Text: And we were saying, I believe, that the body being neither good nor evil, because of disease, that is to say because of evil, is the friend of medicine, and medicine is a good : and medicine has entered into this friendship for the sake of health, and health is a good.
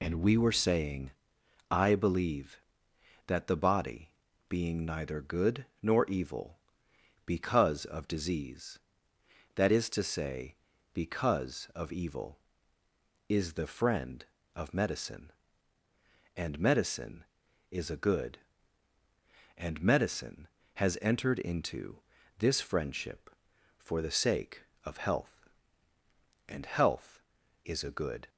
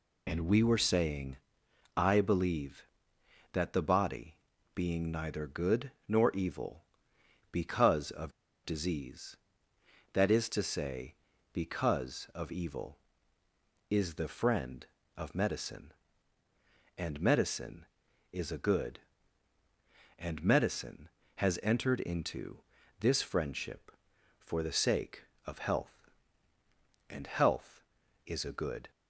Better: first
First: pauses between "body" and "being"; at 4.1 s; 0.38 s long // pauses between "good" and "nor"; slight; at 5.6 s; 0.16 s long // pauses between "into" and "this"; at 21.9 s; 0.40 s long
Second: pauses between "body" and "being"; at 4.3 s; 0.38 s long // pauses between "good" and "nor"; slight; at 5.8 s; 0.16 s long // pauses between "of" and "disease"; slight; at 8.3 s; 0.33 s long // pauses between "into" and "this"; at 22.5 s; 0.40 s long

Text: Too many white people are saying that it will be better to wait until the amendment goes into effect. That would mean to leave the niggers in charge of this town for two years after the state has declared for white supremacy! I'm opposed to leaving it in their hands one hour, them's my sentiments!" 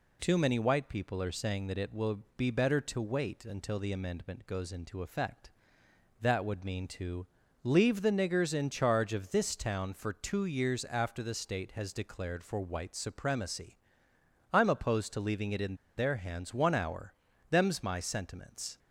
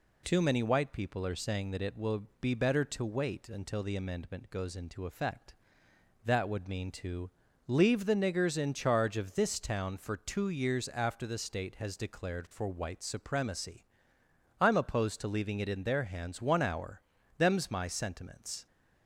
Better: second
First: pauses between "will" and "be"; slight; at 2.2 s; 0.16 s long // pauses between "to" and "leave"; slight; at 7.2 s; 0.36 s long // pauses between "in" and "their"; slight; at 15.7 s; 0.20 s long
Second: pauses between "will" and "be"; slight; at 2.2 s; 0.16 s long // pauses between "to" and "leave"; slight; at 7.3 s; 0.36 s long

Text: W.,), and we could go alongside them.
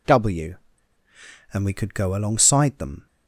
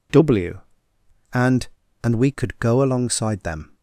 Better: first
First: none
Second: says "and" twice; at 2.0 s

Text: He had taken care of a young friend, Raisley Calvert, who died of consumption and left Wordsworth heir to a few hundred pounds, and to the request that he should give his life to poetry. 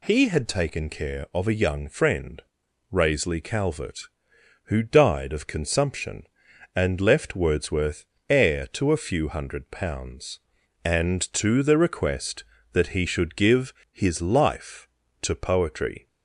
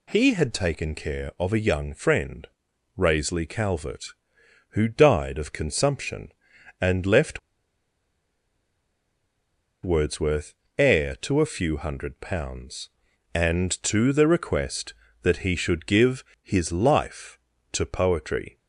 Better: first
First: pauses between "Wordsworth" and "heir"; slight; at 8.0 s; 0.26 s long // pauses between "give" and "his"; slight; at 13.7 s; 0.18 s long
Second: pauses between "left" and "Wordsworth"; strong; at 7.3 s; 2.4 s long // pauses between "Wordsworth" and "heir"; slight; at 10.5 s; 0.26 s long // pauses between "give" and "his"; slight; at 16.2 s; 0.18 s long

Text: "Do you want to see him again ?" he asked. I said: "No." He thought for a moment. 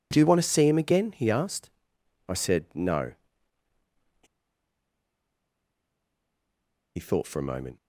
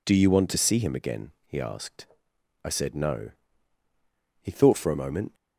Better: second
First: pauses between "He" and "thought"; strong; at 4.2 s; 2.7 s long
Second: none

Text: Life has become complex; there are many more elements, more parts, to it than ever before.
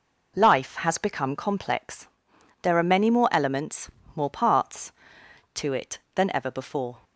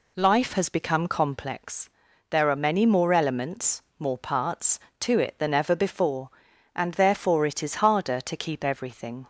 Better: first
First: none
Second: goes on to say "And therefore it is harder to keep everything"; strong; from 6.7 s on; 2.5 s long

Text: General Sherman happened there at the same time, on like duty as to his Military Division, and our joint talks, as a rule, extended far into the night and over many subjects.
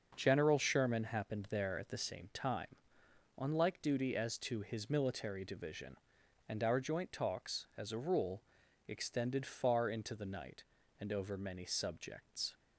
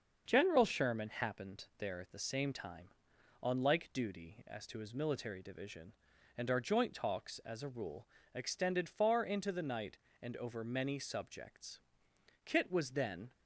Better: first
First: starts louder than the rest; noticeable; until 1.1 s; 6 dB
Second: starts louder than the rest; until 1.2 s; 6.5 dB // goes on to say "Kit was then"; noticeable; from 12.4 s on; 0.86 s long

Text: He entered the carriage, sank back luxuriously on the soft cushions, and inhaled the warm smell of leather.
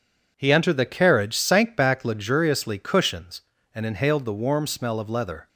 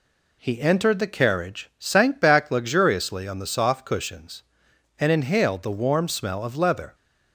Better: second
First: skips "on the soft"; at 2.7 s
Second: none

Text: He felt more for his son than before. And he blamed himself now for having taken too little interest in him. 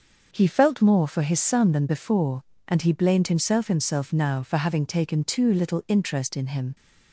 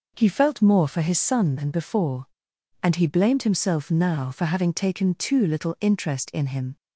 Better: second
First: starts louder than the rest; until 1.3 s; 6.5 dB // says "himself" twice; at 3.6 s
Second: none

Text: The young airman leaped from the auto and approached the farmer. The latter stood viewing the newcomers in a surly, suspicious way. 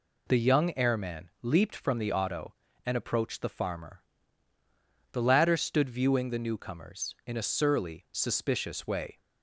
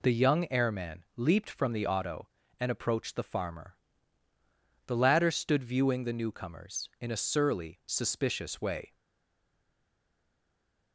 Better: first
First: none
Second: stays silent after the last word; noticeable; from 8.9 s on; 2.0 s long

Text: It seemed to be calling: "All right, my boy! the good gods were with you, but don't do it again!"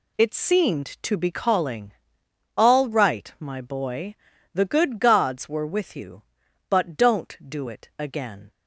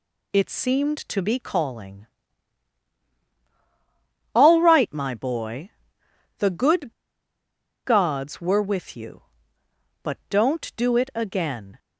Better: first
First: none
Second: pauses between "good" and "gods"; noticeable; at 6.9 s; 0.92 s long

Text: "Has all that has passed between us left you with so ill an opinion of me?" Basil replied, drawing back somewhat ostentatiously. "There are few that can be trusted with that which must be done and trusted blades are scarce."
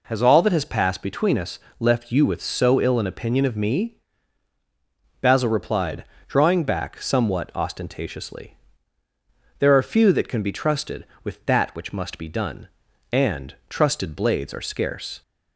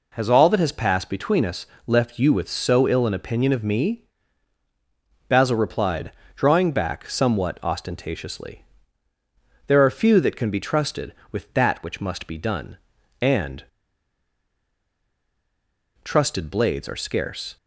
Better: first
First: pauses between "us" and "left"; slight; at 1.5 s; 0.22 s long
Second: pauses between "us" and "left"; slight; at 1.6 s; 0.22 s long // pauses between "and" and "trusted"; strong; at 13.6 s; 2.3 s long

